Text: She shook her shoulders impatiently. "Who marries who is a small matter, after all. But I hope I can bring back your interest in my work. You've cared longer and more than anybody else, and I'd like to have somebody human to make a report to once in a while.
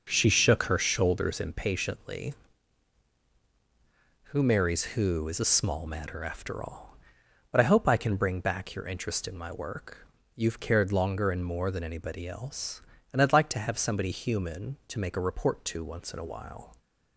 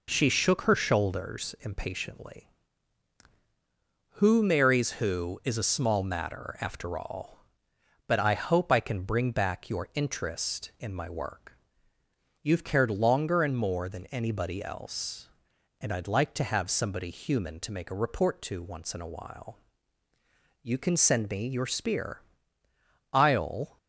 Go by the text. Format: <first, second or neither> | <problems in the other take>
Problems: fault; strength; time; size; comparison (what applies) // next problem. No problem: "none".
first | goes on to say "You can send me your spear I'll"; strong; from 20.6 s on; 3.1 s long